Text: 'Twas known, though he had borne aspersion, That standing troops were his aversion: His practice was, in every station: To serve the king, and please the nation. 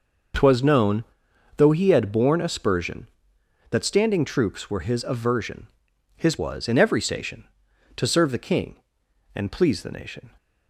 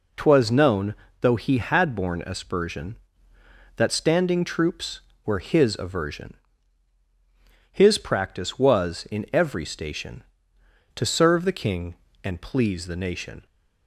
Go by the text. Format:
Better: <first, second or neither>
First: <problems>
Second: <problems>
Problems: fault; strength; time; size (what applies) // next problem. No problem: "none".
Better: second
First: skips "practice"; at 6.3 s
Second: none